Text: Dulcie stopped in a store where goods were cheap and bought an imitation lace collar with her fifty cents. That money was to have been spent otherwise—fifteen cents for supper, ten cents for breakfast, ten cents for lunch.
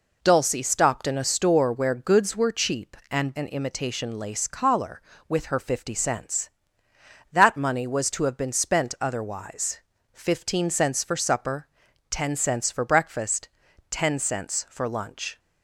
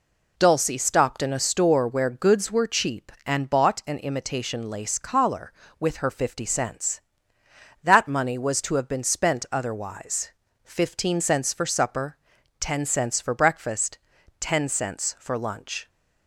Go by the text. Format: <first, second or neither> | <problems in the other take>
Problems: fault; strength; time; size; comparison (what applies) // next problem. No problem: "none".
second | skips "bought"; at 3.3 s